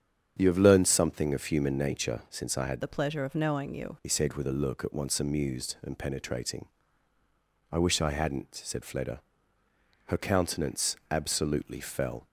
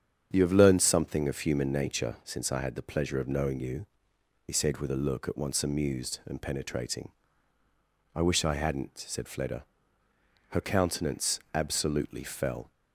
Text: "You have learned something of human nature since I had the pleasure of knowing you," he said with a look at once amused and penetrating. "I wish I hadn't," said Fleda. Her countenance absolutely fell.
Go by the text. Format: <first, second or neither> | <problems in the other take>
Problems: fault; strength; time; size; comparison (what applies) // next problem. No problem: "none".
second | starts louder than the rest; strong; until 1.3 s; 8 dB; strong in the second // changes voice from "the" to "you"; from 2.8 to 3.9 s; 1.1 s long